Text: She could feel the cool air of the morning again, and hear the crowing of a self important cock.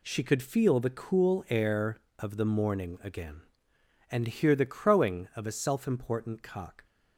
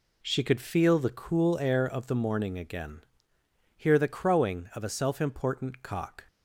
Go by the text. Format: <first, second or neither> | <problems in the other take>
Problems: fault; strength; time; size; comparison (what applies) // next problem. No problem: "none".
first | skips "and"; at 3.3 s